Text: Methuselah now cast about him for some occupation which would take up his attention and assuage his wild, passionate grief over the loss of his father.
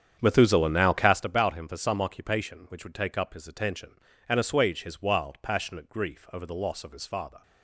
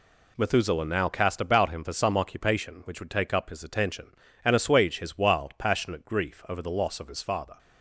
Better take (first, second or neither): second